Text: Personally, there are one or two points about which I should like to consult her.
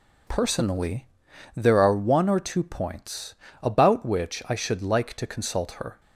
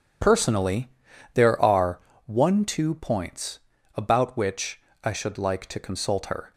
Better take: first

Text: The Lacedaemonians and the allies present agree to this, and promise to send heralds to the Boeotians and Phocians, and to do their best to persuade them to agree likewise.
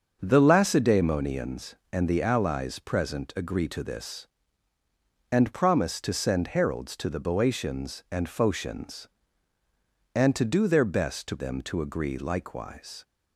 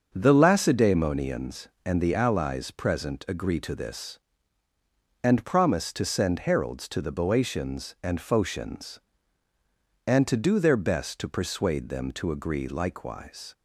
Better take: second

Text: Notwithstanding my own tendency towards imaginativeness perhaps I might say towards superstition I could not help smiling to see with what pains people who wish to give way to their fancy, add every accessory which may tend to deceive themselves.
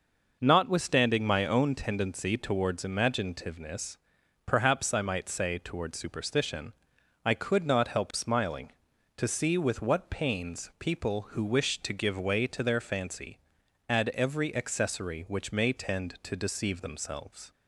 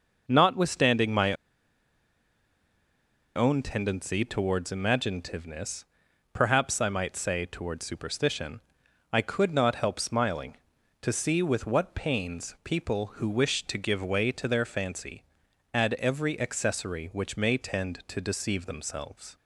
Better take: first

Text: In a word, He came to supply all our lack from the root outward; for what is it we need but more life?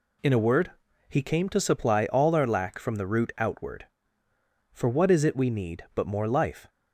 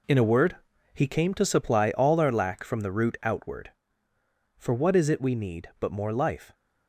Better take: first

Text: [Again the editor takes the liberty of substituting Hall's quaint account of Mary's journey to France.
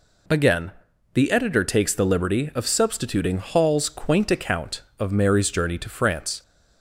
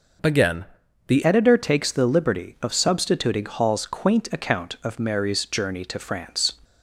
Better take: first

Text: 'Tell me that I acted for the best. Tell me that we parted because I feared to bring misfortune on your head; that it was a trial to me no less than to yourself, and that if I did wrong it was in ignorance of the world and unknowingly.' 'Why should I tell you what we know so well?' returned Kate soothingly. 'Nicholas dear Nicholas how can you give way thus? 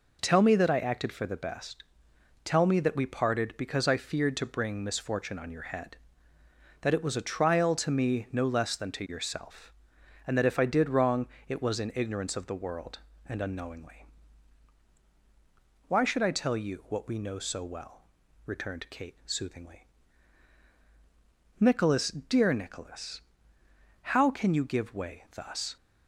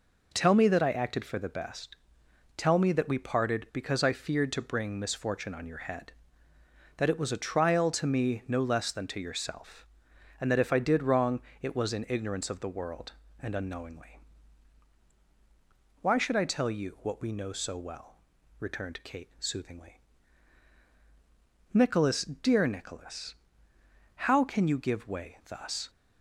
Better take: neither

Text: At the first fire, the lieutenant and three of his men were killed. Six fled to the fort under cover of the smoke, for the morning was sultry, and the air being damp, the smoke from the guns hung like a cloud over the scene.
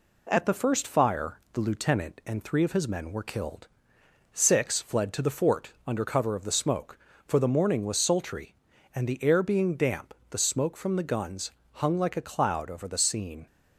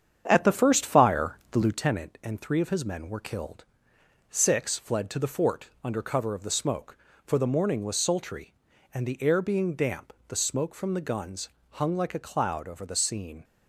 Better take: first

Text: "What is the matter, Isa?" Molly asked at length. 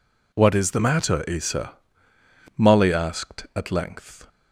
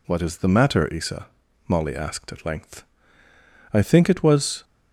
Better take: first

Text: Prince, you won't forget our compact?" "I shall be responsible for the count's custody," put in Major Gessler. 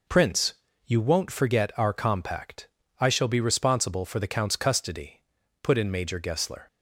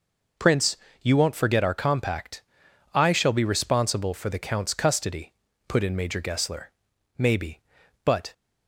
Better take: first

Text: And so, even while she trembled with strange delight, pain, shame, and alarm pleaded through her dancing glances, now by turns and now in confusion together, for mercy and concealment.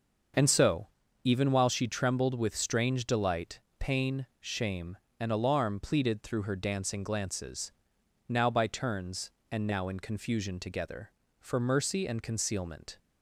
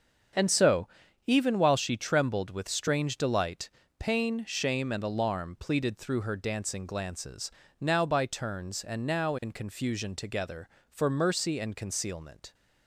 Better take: neither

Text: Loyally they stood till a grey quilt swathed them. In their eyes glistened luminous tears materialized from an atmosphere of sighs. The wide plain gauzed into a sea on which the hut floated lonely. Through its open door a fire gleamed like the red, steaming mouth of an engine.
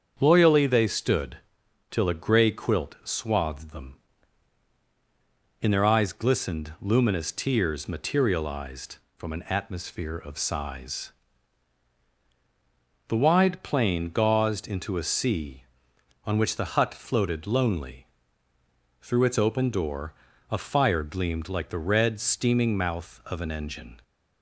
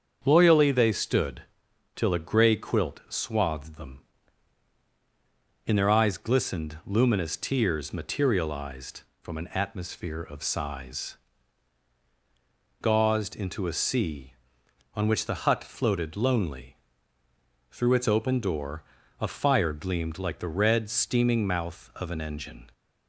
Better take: first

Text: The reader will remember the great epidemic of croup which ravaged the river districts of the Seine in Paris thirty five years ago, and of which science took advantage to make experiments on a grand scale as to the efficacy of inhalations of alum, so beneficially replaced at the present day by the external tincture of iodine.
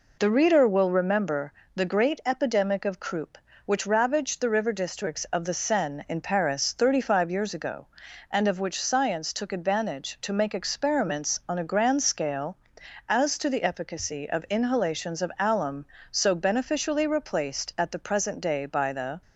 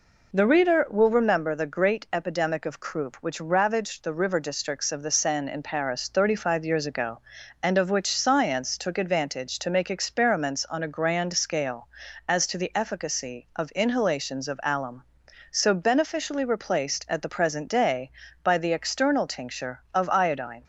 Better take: second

